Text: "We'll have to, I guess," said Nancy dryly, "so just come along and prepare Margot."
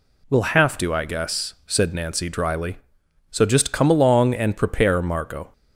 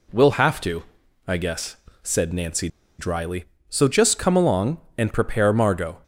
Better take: first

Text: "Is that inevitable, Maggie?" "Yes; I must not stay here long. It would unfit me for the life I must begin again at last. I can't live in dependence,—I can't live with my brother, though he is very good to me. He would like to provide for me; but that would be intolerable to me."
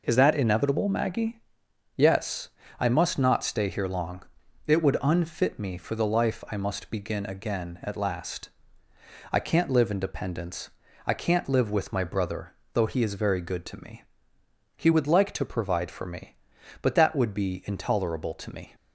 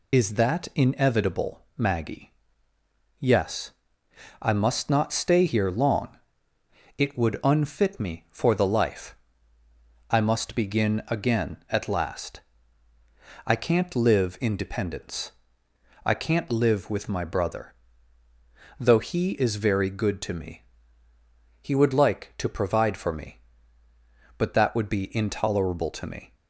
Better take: first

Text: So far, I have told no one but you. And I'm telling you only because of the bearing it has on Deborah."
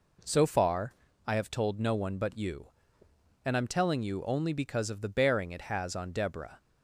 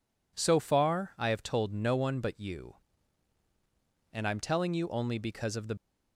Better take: first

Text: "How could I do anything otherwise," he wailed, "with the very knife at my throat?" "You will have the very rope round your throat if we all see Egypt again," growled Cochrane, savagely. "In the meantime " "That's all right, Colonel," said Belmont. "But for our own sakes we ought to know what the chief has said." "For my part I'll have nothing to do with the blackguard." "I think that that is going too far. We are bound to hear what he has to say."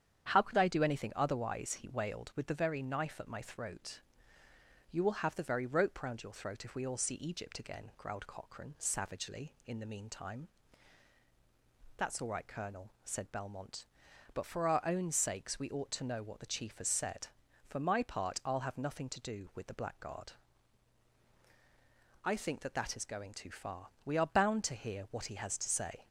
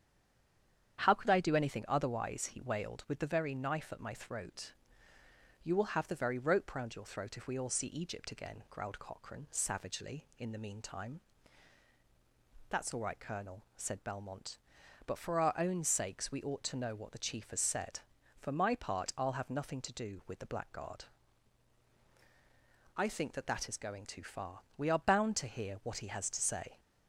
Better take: first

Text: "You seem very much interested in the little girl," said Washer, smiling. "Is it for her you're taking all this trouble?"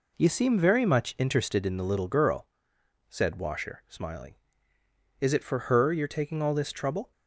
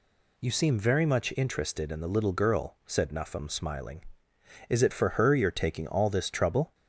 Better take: first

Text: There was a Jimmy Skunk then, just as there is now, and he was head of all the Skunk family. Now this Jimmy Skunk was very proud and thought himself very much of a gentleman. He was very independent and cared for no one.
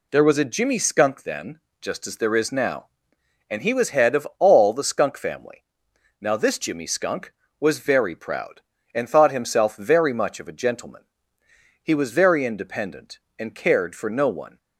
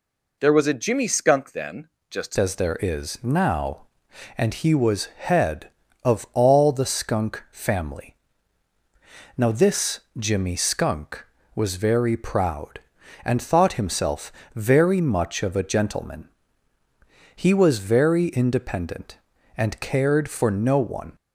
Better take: first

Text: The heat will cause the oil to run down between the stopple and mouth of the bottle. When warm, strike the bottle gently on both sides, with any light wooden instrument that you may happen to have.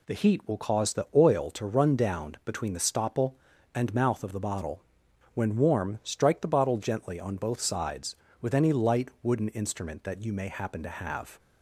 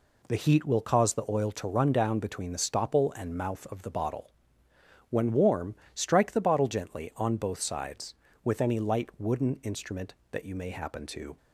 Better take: first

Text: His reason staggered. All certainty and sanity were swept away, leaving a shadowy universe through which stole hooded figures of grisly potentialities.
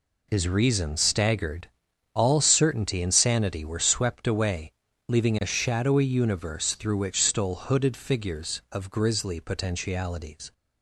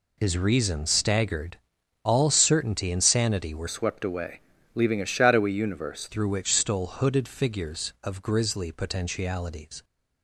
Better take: first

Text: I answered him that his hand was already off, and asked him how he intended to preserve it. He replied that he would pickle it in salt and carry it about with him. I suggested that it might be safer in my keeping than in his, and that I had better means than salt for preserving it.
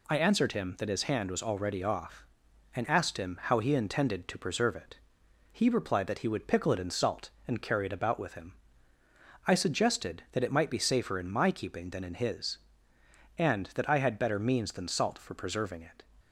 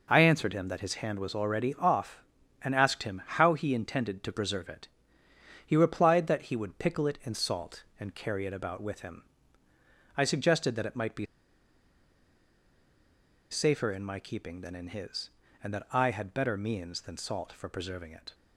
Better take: first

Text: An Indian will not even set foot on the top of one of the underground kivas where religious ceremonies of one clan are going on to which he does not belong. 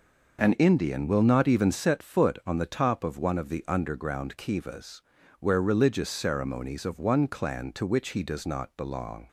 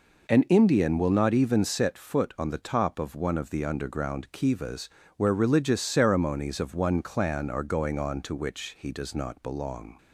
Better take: second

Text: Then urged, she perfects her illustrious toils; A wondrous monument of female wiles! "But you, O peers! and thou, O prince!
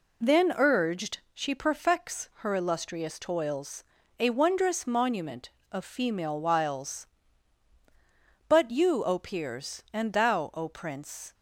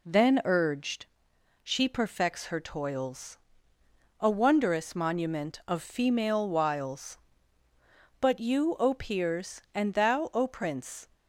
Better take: first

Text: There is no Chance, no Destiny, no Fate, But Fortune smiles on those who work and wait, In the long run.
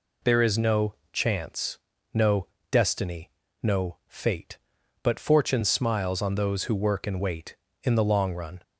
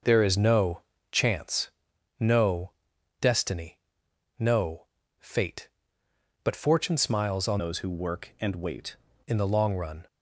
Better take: first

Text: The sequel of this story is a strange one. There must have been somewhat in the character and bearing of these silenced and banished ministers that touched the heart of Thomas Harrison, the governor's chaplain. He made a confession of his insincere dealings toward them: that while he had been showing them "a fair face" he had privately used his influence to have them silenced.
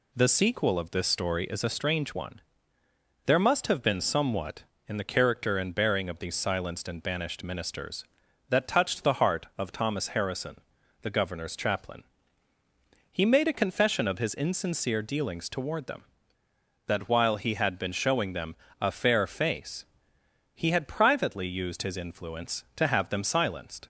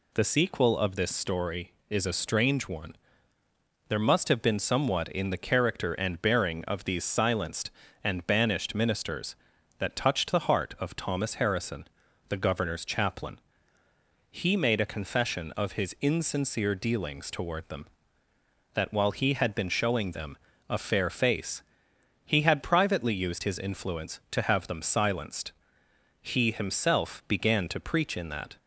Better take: first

